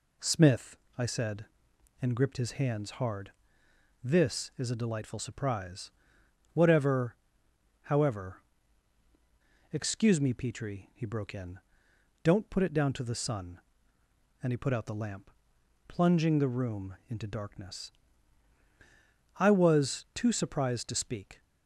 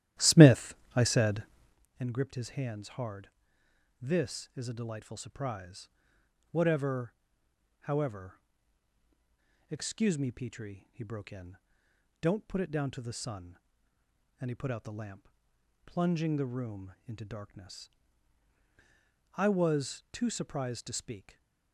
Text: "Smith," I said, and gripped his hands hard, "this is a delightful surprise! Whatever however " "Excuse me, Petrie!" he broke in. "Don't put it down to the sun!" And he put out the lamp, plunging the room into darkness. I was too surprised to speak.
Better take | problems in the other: first | starts louder than the rest; strong; until 1.8 s; 13 dB // pauses between "Whatever" and "however"; noticeable; at 7.1 s; 0.68 s long; noticeable in the first // stays silent after the last word; slight; from 21.1 s on; 0.6 s long

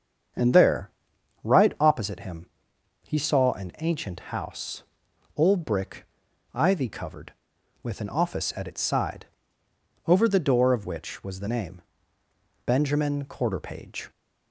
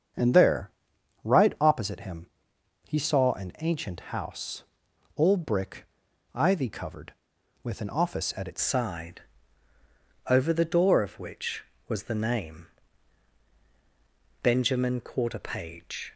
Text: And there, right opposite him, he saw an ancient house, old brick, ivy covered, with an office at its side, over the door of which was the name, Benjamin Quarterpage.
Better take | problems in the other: first | starts louder than the rest; strong; until 1.7 s; 7.5 dB; strong in the first // changes voice at "side"; from 8.6 s on; 7.5 s long

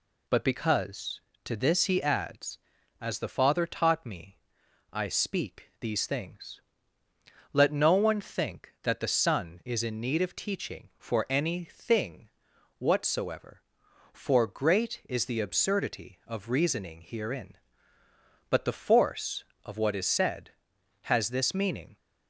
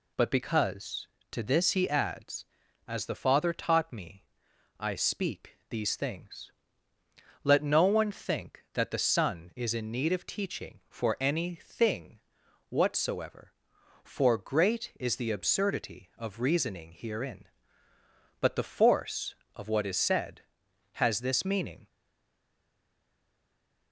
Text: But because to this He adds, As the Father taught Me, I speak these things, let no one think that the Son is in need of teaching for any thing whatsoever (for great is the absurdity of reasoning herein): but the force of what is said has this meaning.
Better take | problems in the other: first | pauses between "thing" and "whatsoever"; noticeable; at 12.1 s; 0.52 s long; noticeable in the first // stays silent after the last word; noticeable; from 21.8 s on; 2.1 s long

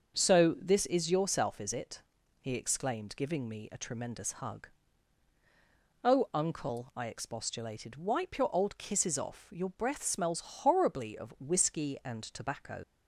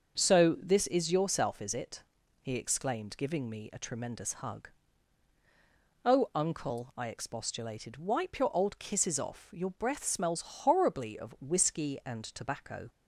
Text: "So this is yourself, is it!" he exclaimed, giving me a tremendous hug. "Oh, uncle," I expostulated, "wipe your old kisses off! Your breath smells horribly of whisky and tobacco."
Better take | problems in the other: second | starts louder than the rest; until 1.2 s; 6.5 dB; also in the second // leaves "tobacco" unfinished; at 12.8 s; 50 ms

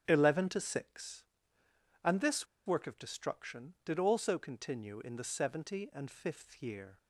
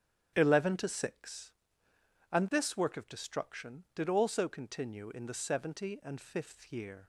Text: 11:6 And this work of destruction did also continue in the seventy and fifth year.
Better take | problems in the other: second | starts louder than the rest; strong; until 1.0 s; 9.5 dB; strong in the second // pauses between "this" and "work"; slight; at 2.4 s; 0.20 s long

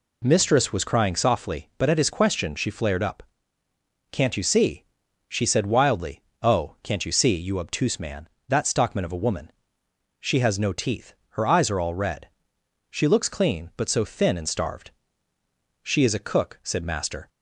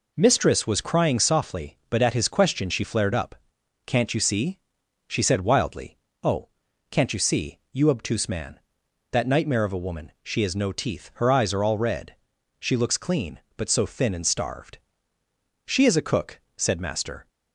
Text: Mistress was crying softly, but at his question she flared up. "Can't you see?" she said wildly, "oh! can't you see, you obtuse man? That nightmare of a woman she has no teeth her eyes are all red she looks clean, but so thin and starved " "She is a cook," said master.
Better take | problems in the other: second | says "stockman" for "nightmare"; at 8.6 s // pauses between "woman" and "she"; noticeable; at 9.5 s; 0.70 s long // pauses between "teeth" and "her"; slight; at 11.1 s; 0.16 s long // pauses between "red" and "she"; noticeable; at 12.2 s; 0.60 s long; also in the second

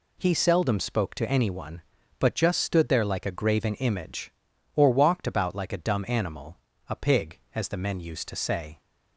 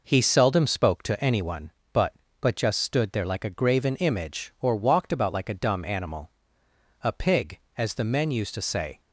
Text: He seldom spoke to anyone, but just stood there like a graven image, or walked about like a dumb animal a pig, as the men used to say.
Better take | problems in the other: first | says "but" twice; at 2.3 s // pauses between "animal" and "a"; noticeable; at 6.2 s; 0.72 s long; slight in the first

